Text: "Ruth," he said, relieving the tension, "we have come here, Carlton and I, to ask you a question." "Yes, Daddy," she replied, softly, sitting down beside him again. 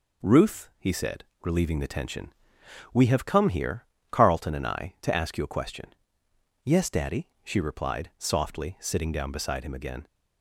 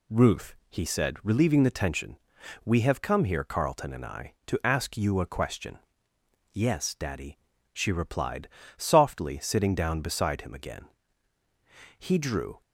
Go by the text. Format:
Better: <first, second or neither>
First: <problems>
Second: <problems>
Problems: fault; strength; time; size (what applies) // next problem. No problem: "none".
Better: first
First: none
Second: goes on to say "He drew"; noticeable; from 11.9 s on; 0.62 s long